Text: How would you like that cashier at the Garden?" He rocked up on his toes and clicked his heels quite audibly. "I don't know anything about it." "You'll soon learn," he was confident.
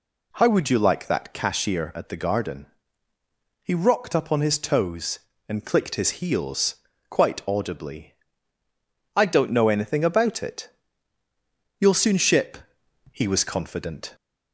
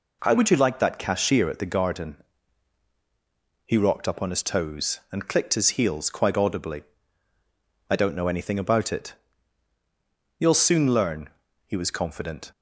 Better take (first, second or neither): second